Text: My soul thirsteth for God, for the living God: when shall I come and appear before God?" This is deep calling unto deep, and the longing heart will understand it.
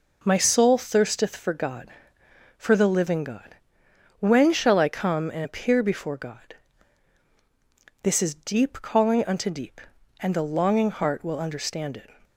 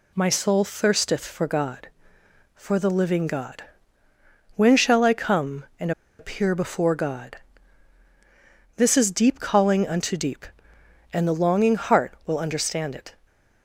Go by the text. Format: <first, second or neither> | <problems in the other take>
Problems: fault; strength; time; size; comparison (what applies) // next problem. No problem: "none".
first | pauses between "and" and "appear"; slight; at 5.9 s; 0.28 s long